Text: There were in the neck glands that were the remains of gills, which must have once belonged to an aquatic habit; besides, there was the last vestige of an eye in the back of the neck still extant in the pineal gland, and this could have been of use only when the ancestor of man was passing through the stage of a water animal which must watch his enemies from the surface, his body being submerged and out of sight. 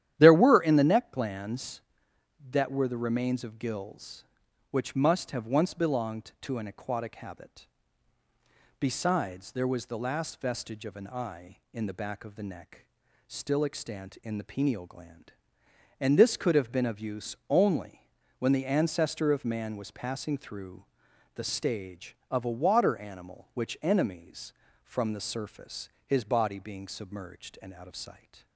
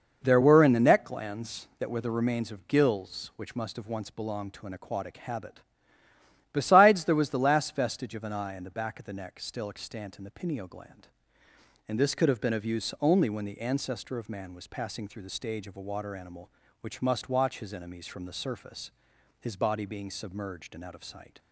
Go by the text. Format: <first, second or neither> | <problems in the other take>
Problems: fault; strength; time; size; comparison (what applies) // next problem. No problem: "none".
second | starts louder than the rest; strong; until 1.1 s; 11 dB // pauses between "neck" and "still"; at 12.8 s; 0.42 s long // pauses between "only" and "when"; slight; at 18.0 s; 0.32 s long // pauses between "through" and "the"; noticeable; at 20.8 s; 0.48 s long // skips "must watch his"; at 23.7 s